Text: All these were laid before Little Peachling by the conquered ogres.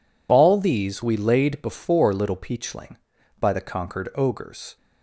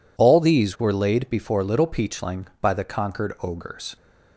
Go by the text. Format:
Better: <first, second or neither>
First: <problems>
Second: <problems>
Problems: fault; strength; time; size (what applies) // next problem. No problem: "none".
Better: second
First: says "we" for "were"; at 1.0 s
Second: none